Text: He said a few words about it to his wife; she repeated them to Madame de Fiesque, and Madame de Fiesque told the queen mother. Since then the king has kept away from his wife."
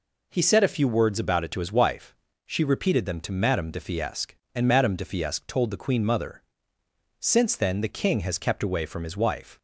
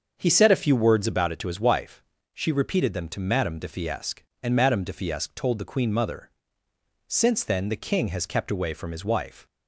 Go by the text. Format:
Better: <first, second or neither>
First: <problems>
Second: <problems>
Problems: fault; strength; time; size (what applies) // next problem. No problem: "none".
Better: first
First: none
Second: starts louder than the rest; until 1.3 s; 6.5 dB